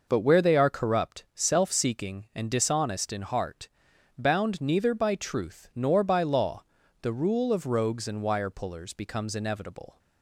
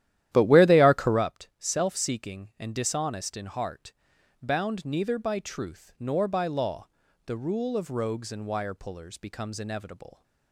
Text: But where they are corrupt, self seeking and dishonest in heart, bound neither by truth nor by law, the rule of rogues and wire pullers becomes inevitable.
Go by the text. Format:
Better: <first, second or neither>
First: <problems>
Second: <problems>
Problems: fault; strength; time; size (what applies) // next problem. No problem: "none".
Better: first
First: none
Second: starts louder than the rest; strong; until 1.3 s; 12.5 dB